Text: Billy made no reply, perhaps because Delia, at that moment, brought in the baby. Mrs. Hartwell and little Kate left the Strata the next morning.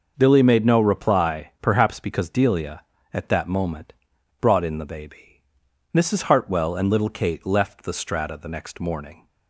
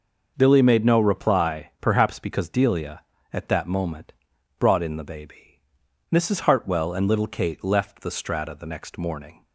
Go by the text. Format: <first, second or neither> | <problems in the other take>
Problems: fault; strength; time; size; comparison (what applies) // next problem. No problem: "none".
neither | none